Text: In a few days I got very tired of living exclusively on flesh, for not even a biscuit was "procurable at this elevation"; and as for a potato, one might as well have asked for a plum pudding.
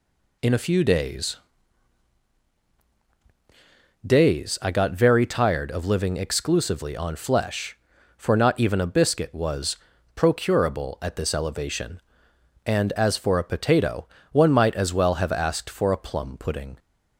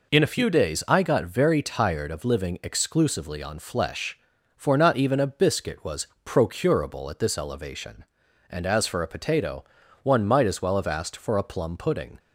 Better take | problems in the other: second | says "days" twice; at 4.0 s // pauses between "was" and "procurable"; at 9.7 s; 0.40 s long; slight in the second

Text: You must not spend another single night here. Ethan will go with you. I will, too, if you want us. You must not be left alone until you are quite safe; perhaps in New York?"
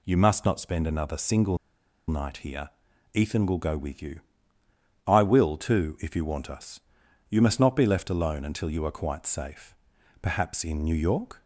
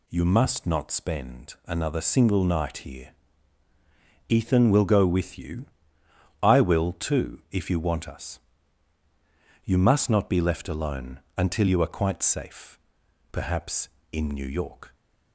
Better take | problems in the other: second | pauses between "single" and "night"; noticeable; at 1.5 s; 0.51 s long

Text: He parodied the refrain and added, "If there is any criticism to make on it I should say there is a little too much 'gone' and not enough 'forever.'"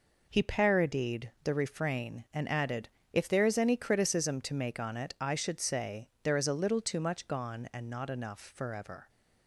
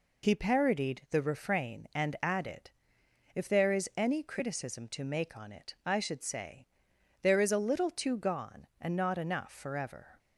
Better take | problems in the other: first | pauses between "say" and "there"; noticeable; at 6.6 s; 0.54 s long // skips "much"; at 8.1 s

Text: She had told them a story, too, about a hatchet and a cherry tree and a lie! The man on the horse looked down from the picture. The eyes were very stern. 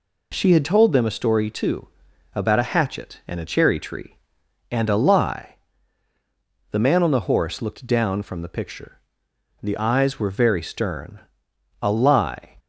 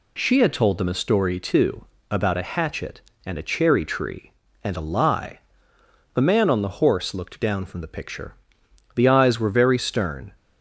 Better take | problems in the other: second | goes on to say "A lie"; noticeable; from 11.8 s on; 0.74 s long

